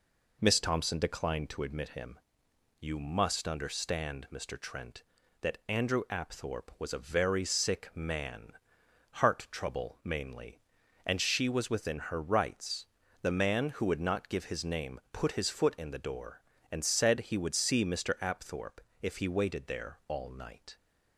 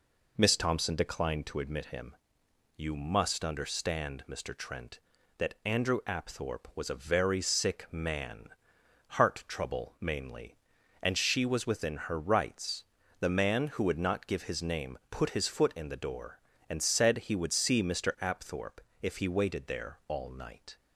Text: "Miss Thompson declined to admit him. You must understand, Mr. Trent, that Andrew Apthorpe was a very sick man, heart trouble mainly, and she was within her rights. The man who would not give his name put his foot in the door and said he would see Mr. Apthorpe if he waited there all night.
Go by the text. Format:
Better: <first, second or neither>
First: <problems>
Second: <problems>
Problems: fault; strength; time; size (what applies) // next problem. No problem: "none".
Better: neither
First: pauses between "Apthorpe" and "if"; slight; at 18.8 s; 0.20 s long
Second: pauses between "Apthorpe" and "if"; slight; at 18.8 s; 0.20 s long